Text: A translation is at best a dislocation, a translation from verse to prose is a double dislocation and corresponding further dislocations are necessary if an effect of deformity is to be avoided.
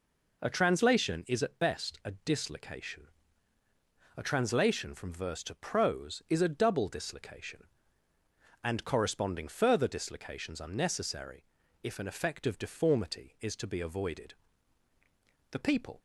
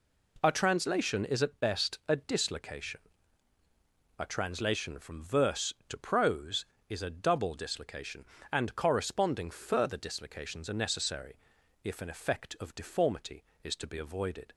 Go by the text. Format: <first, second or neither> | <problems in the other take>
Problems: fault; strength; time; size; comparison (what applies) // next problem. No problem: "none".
second | pauses between "necessary" and "if"; at 11.4 s; 0.40 s long; noticeable in the second // goes on to say "The people"; slight; from 15.5 s on; 0.48 s long